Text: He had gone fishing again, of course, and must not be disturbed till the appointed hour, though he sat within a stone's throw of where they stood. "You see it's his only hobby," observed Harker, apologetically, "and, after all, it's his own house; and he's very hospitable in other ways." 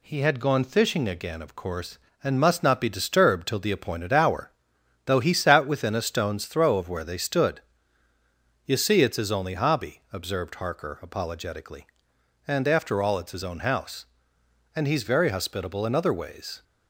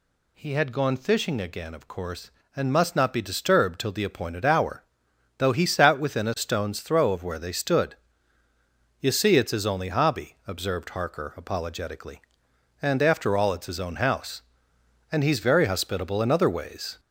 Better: first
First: none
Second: gets louder; slight; throughout; 2.5 dB

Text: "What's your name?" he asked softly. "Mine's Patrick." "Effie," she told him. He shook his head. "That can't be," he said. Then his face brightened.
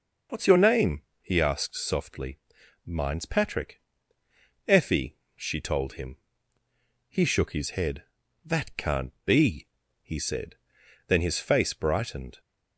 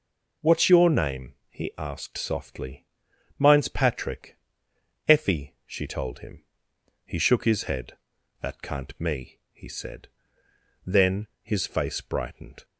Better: first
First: none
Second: says "me" for "be"; at 8.9 s // pauses between "Then" and "his"; slight; at 11.2 s; 0.16 s long

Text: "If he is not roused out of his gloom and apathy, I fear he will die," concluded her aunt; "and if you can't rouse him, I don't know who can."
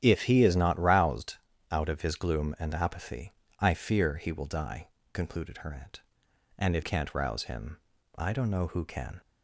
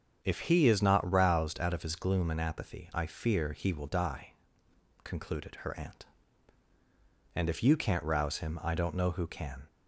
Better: second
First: starts louder than the rest; strong; until 1.0 s; 10.5 dB // pauses between "roused" and "out"; slight; at 1.3 s; 0.34 s long // skips "you"; at 6.8 s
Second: starts louder than the rest; strong; until 1.2 s; 7.5 dB

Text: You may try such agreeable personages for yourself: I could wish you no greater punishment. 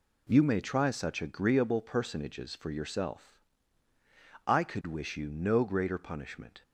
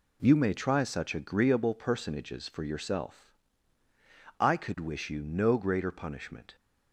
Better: neither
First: none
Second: none

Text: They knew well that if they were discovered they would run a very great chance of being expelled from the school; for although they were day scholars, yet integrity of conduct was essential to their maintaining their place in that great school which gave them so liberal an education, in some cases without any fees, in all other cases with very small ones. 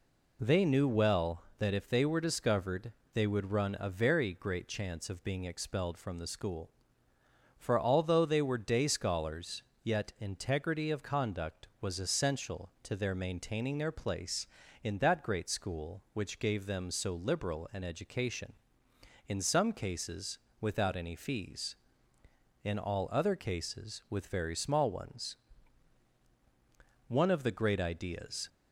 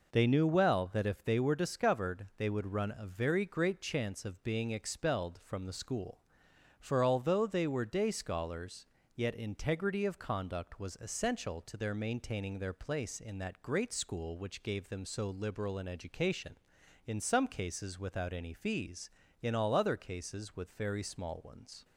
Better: second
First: pauses between "discovered" and "they"; slight; at 2.9 s; 0.20 s long // pauses between "cases" and "without"; slight; at 20.3 s; 0.20 s long // goes on to say "One of the great ideas"; from 27.0 s on; 1.4 s long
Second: none

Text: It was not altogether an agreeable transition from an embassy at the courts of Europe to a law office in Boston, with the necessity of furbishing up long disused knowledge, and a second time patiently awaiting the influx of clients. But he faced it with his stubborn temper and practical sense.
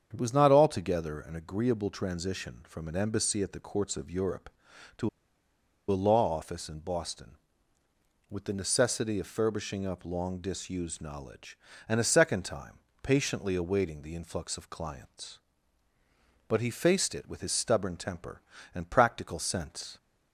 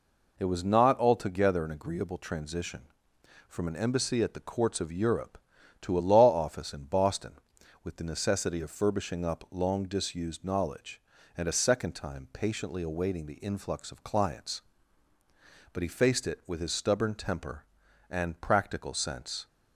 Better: second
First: starts louder than the rest; strong; until 1.1 s; 7.5 dB // pauses between "to" and "a"; noticeable; at 5.0 s; 0.81 s long // pauses between "time" and "patiently"; slight; at 12.7 s; 0.24 s long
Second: none

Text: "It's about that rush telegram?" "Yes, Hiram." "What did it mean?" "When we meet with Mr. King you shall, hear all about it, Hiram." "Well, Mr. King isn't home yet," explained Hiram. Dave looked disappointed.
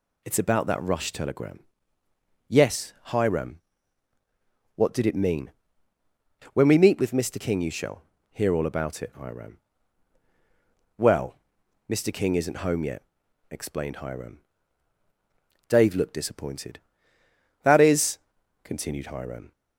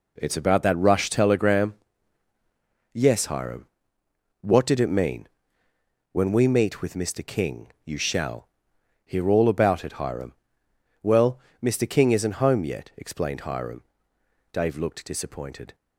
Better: second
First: goes on to say "That is continued Hiram"; strong; from 17.6 s on; 1.9 s long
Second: none

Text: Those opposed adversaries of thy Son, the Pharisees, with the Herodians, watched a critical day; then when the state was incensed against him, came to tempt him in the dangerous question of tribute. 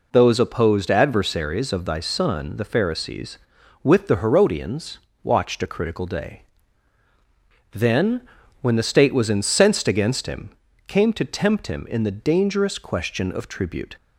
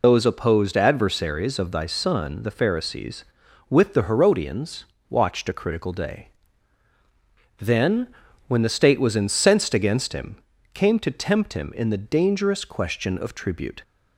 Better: first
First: pauses between "then" and "when"; at 8.2 s; 0.40 s long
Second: loses the start of "Those"; at 0.0 s; 55 ms // pauses between "then" and "when"; at 8.0 s; 0.40 s long

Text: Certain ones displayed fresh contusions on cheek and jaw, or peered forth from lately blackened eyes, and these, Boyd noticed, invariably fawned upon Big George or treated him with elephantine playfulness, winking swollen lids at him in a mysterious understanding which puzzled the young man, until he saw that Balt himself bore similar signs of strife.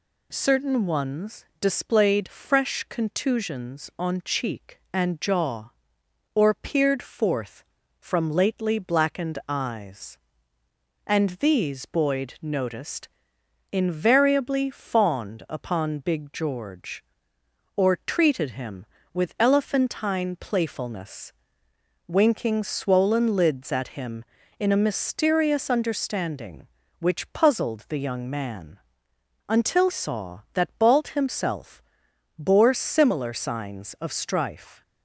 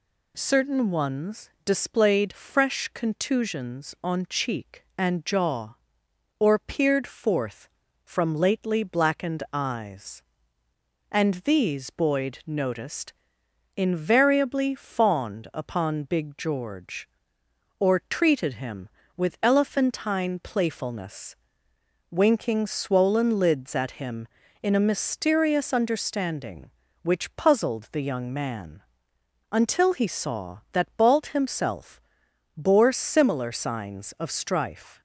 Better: second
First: pauses between "ones" and "displayed"; slight; at 1.4 s; 0.16 s long // skips "he"; at 29.8 s // pauses between "himself" and "bore"; noticeable; at 31.8 s; 0.56 s long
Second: pauses between "ones" and "displayed"; slight; at 1.4 s; 0.16 s long // pauses between "himself" and "bore"; noticeable; at 32.0 s; 0.56 s long

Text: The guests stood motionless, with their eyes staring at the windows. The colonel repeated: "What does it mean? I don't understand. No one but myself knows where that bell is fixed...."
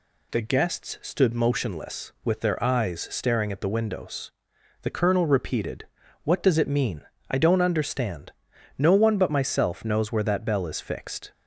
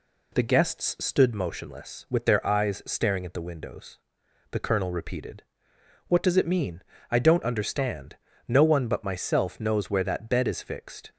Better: first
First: none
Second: says "bed" for "bell"; at 10.2 s

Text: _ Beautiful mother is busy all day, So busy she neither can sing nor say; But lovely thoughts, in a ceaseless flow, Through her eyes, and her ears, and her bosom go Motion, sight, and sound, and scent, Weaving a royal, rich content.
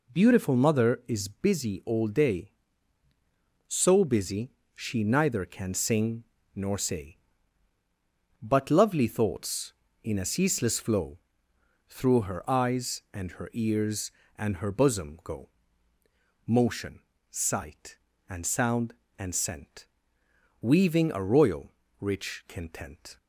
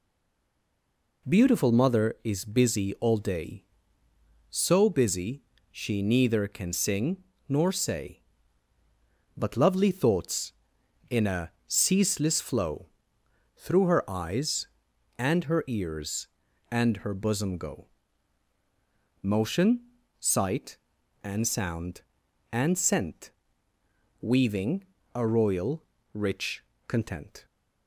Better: first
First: pauses between "busy" and "she"; slight; at 4.5 s; 0.22 s long // pauses between "sing" and "nor"; slight; at 6.2 s; 0.32 s long // pauses between "go" and "Motion"; noticeable; at 15.4 s; 0.98 s long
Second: stays silent before the first word; noticeable; until 1.2 s; 1.2 s long // pauses between "busy" and "she"; slight; at 5.4 s; 0.28 s long // pauses between "sing" and "nor"; slight; at 7.1 s; 0.28 s long // pauses between "a" and "ceaseless"; slight; at 11.5 s; 0.16 s long // pauses between "go" and "Motion"; strong; at 17.8 s; 1.3 s long // pauses between "Weaving" and "a"; slight; at 24.8 s; 0.29 s long // pauses between "rich" and "content"; slight; at 26.6 s; 0.24 s long

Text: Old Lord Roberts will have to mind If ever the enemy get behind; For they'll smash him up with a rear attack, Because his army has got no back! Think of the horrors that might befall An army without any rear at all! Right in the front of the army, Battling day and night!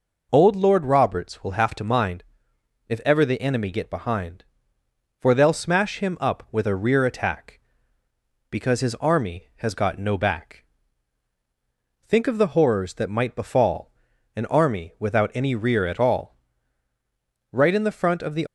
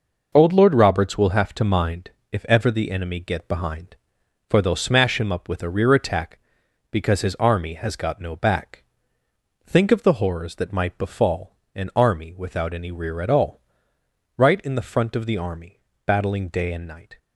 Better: second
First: pauses between "mind" and "If"; noticeable; at 2.2 s; 0.64 s long // pauses between "befall" and "An"; at 13.9 s; 0.42 s long // stops before "army Battling day and night"; at 18.4 s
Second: pauses between "mind" and "If"; slight; at 2.0 s; 0.22 s long // pauses between "befall" and "An"; slight; at 11.5 s; 0.20 s long

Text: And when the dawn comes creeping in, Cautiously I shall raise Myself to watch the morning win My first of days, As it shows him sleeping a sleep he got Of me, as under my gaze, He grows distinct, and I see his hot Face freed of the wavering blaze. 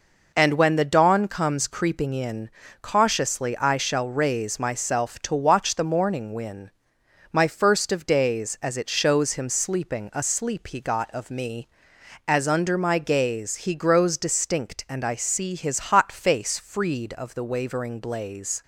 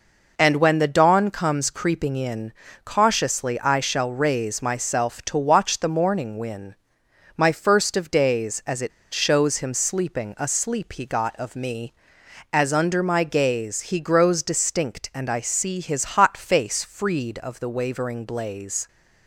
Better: first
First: pauses between "win" and "My"; noticeable; at 6.7 s; 0.62 s long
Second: pauses between "win" and "My"; noticeable; at 6.7 s; 0.62 s long // pauses between "it" and "shows"; slight; at 8.9 s; 0.22 s long

